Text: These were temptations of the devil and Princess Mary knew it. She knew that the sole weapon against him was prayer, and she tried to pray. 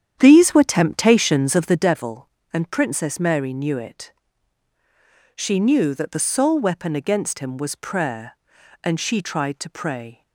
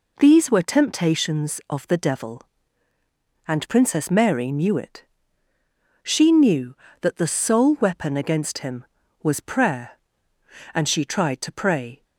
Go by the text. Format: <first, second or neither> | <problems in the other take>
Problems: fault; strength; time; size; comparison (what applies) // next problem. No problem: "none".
second | starts louder than the rest; strong; until 1.9 s; 9 dB